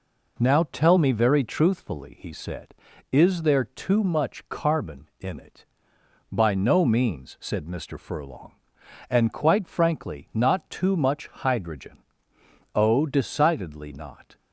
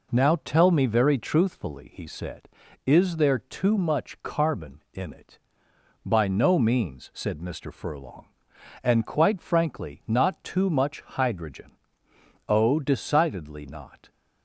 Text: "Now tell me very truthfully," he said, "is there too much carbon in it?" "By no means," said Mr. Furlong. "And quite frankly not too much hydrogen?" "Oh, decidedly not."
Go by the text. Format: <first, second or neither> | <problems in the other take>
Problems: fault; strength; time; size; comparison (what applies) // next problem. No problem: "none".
neither | none